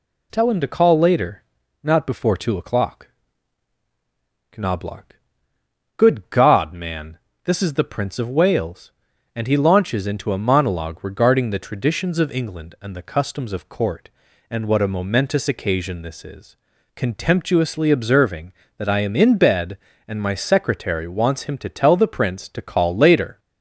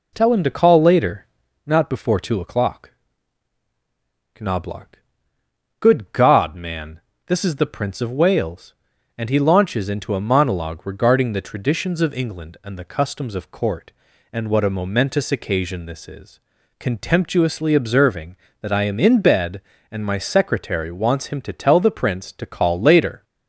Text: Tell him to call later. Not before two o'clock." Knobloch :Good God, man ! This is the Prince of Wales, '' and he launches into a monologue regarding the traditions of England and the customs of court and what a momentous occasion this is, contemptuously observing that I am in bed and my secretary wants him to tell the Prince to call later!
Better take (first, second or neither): first